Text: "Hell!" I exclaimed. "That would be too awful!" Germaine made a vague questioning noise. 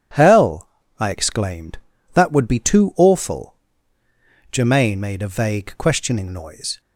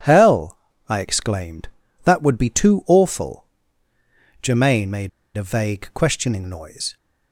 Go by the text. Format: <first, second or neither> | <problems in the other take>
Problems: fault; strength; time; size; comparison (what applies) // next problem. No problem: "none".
first | pauses between "made" and "a"; slight; at 5.0 s; 0.26 s long